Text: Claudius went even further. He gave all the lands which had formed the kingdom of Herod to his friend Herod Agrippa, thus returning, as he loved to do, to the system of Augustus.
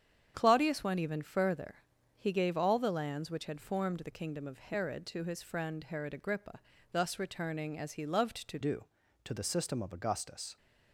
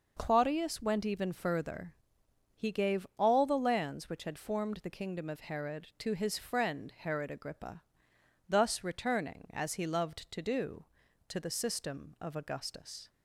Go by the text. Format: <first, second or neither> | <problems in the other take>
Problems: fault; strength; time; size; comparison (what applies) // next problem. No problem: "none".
second | starts louder than the rest; strong; until 1.3 s; 8.5 dB // changes voice at "do"; from 8.6 s on; 1.9 s long